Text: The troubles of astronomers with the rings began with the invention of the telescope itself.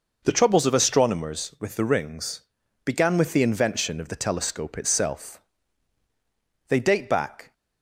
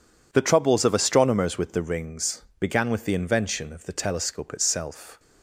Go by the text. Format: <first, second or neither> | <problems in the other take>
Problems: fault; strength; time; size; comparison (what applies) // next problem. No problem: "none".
second | pauses between "rings" and "began"; at 2.4 s; 0.44 s long; slight in the second // goes on to say "They date back"; noticeable; from 6.6 s on; 0.84 s long